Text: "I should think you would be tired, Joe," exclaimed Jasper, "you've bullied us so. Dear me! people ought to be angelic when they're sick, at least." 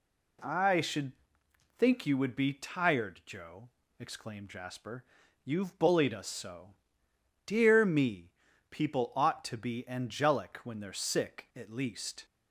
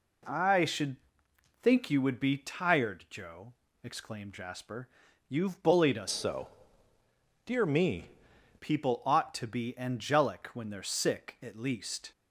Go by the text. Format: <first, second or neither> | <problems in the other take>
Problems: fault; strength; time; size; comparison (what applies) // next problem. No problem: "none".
first | pauses between "should" and "think"; noticeable; at 0.9 s; 0.66 s long; noticeable in the first // changes voice from "so" to "me"; from 6.1 to 8.1 s; 2.0 s long